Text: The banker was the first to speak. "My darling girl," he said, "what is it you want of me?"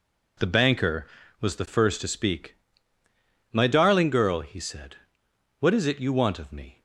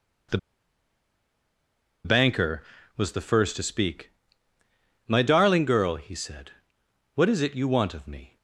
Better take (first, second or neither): first